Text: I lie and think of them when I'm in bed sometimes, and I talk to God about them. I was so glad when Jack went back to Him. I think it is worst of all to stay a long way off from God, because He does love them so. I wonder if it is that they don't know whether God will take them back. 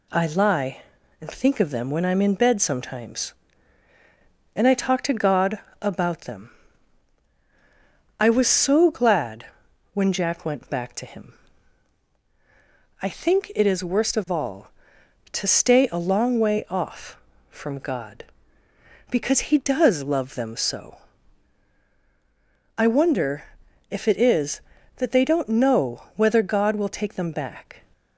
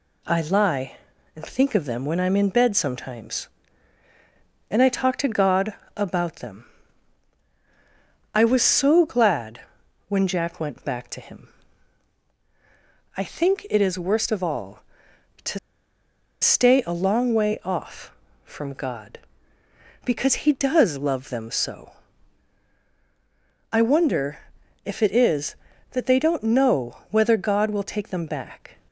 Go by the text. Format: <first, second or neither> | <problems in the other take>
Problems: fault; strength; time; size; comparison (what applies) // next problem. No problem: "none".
first | pauses between "God" and "about"; slight; at 5.7 s; 0.24 s long; slight in the first // pauses between "glad" and "when"; noticeable; at 9.5 s; 0.48 s long; noticeable in the first // pauses between "to" and "stay"; noticeable; at 15.5 s; 0.82 s long // pauses between "wonder" and "if"; at 24.3 s; 0.44 s long; also in the first